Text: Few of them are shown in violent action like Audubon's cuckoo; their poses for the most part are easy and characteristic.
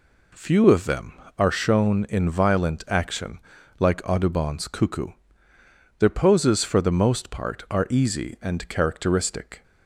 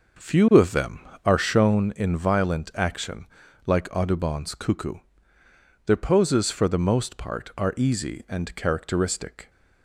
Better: first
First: pauses between "action" and "like"; at 3.3 s; 0.40 s long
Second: starts louder than the rest; noticeable; until 1.9 s; 5 dB // pauses between "action" and "like"; at 3.2 s; 0.40 s long

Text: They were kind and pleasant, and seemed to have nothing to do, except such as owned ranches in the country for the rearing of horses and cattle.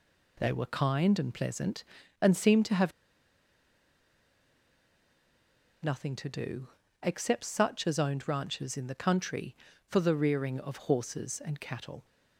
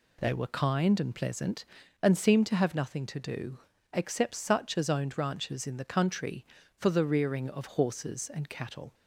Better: second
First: pauses between "have" and "nothing"; strong; at 2.9 s; 2.9 s long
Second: none

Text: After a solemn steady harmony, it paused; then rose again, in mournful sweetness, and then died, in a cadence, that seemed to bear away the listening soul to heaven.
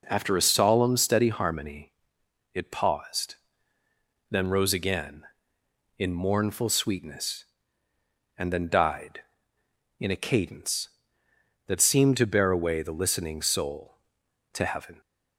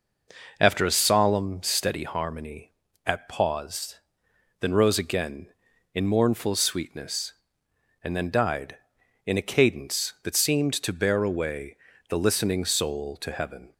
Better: first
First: none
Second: says "at" for "it"; at 3.0 s // pauses between "away" and "the"; slight; at 11.7 s; 0.32 s long

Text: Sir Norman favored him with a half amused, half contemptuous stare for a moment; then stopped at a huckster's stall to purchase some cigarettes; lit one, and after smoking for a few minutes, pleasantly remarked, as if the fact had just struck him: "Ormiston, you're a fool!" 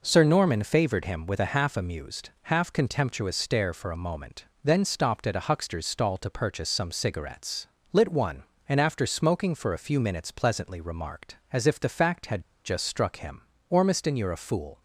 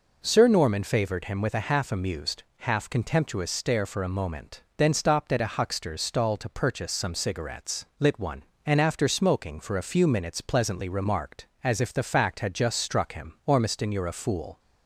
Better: second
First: pauses between "had" and "just"; slight; at 12.4 s; 0.22 s long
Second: none

